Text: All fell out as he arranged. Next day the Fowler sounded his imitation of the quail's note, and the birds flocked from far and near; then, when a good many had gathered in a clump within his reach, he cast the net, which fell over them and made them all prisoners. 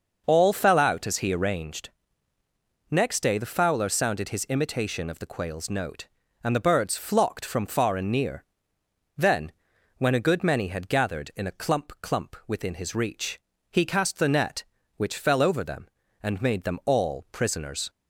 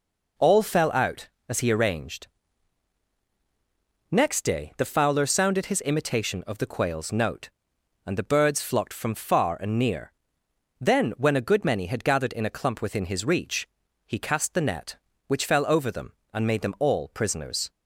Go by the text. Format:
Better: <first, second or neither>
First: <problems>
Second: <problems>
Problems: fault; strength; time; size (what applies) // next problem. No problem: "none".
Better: second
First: starts louder than the rest; noticeable; until 1.2 s; 6 dB // says "clump" twice; at 11.9 s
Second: none